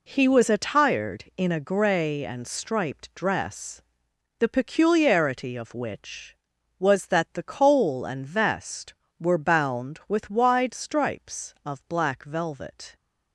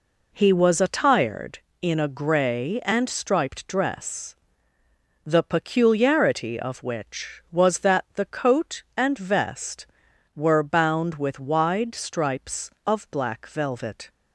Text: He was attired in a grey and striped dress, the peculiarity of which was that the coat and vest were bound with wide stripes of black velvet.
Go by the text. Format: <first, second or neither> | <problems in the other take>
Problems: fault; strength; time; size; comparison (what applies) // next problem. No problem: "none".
second | says "coal" for "coat"; at 7.4 s